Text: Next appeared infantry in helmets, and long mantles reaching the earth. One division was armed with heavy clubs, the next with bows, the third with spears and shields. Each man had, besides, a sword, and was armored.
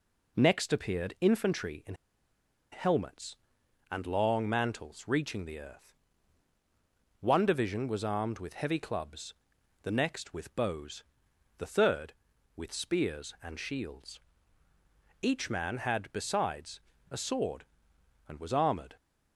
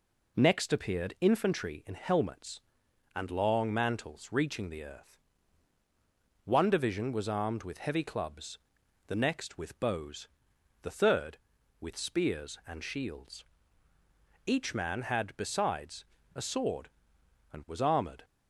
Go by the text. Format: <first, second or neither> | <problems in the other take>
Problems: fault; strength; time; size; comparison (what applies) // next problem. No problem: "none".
second | pauses between "in" and "helmets"; noticeable; at 1.9 s; 0.77 s long